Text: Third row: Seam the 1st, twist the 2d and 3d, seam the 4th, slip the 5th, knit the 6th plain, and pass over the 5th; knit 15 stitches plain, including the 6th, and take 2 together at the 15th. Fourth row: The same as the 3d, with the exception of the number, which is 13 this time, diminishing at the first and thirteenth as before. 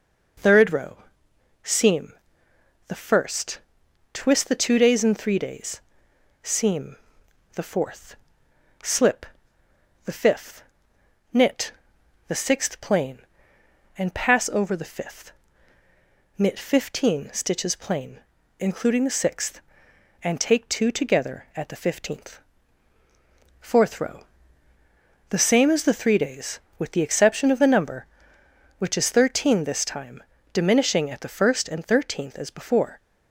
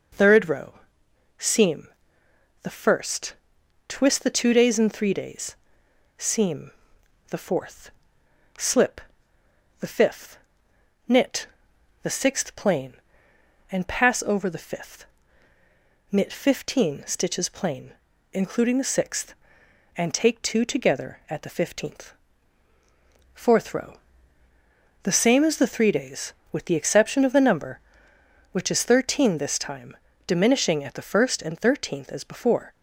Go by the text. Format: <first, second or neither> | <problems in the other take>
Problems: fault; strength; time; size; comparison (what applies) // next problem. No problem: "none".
neither | pauses between "Seam" and "the"; noticeable; the same in both // pauses between "seam" and "the"; noticeable; the same in both // pauses between "slip" and "the"; noticeable; the same in both // pauses between "knit" and "the"; noticeable; the same in both